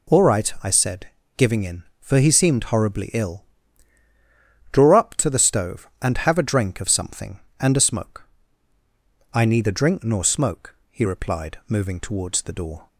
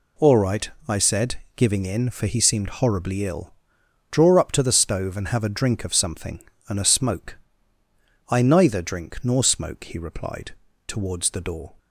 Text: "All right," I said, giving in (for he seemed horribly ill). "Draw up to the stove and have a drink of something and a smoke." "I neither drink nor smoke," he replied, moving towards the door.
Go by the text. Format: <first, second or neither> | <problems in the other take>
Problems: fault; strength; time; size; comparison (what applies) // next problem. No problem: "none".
first | skips "moving"; at 10.7 s